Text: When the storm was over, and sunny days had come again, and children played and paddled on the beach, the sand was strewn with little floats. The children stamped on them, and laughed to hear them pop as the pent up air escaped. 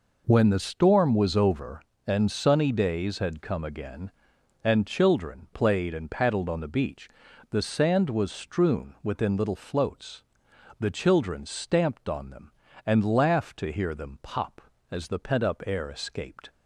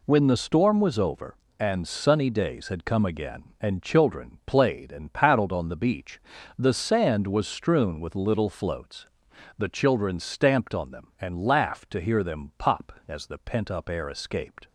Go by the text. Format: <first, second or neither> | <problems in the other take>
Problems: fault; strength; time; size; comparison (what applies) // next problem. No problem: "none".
second | says "within" for "with"; at 9.0 s